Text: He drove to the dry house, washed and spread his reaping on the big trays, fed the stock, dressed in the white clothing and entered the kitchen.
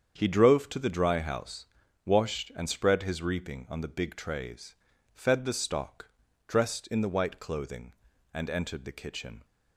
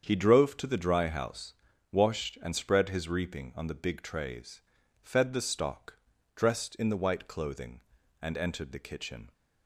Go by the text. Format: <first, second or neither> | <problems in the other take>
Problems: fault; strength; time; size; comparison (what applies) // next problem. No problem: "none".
neither | starts louder than the rest; strong; the same in both